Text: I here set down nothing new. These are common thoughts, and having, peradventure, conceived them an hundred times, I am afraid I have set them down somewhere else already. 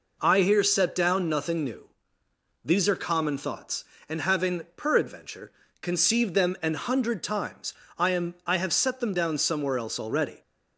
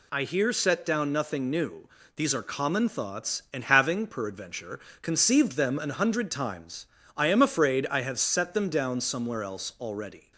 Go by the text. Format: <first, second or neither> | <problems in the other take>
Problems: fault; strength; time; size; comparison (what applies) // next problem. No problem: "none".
second | skips "afraid"; at 8.3 s